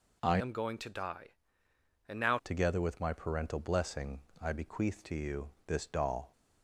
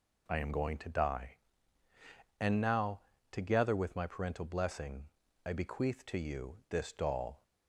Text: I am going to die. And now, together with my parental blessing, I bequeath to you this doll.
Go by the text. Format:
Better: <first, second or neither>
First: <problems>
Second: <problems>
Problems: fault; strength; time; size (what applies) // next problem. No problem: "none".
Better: second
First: changes voice from "am" to "now"; from 0.3 to 2.3 s; 2.0 s long // pauses between "you" and "this"; slight; at 5.4 s; 0.18 s long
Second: none